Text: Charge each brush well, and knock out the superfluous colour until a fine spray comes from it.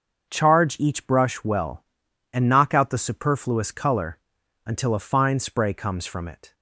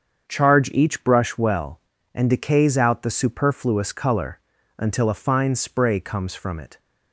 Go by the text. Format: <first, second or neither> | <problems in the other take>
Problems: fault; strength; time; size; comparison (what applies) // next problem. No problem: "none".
first | starts louder than the rest; until 1.3 s; 7 dB; noticeable in the first // says "decays" for "knock"; at 2.2 s // pauses between "colour" and "until"; at 4.3 s; 0.38 s long; noticeable in the first